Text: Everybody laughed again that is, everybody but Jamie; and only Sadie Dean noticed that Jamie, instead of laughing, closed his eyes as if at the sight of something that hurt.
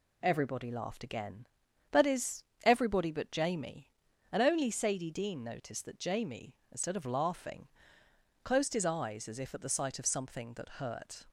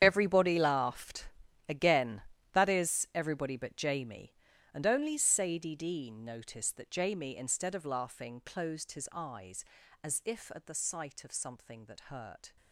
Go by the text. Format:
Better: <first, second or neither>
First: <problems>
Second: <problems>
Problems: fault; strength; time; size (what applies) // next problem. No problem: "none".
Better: first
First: none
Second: gets quieter; strong; throughout; 14.5 dB // pauses between "laughed" and "again"; at 1.2 s; 0.40 s long